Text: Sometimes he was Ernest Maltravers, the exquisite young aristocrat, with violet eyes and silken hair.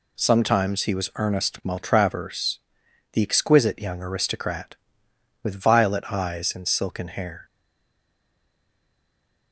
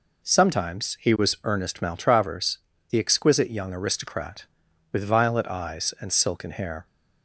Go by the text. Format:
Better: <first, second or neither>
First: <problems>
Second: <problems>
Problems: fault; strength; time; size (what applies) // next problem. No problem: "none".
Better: second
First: stays silent after the last word; noticeable; from 7.4 s on; 2.1 s long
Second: none